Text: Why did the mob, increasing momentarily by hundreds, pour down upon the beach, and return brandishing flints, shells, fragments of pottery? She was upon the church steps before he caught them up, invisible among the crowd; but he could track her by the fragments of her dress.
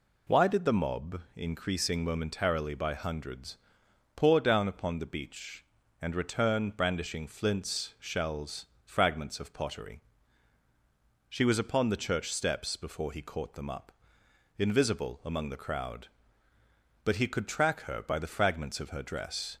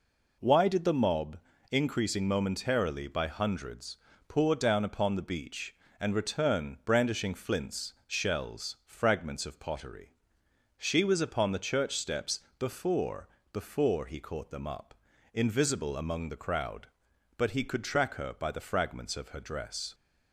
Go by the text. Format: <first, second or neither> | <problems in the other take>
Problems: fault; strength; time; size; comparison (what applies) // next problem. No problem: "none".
first | pauses between "steps" and "before"; slight; at 12.4 s; 0.18 s long // says "before" twice; at 13.5 s